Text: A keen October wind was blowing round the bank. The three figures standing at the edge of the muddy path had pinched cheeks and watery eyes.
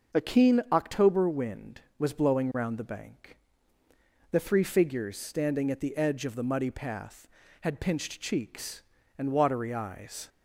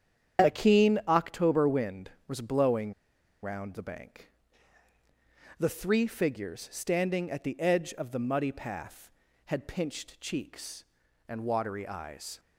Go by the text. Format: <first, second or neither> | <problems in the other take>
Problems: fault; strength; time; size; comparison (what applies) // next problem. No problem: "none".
first | starts louder than the rest; strong; until 1.5 s; 8.5 dB; also in the first // pauses between "blowing" and "round"; noticeable; at 2.9 s; 0.49 s long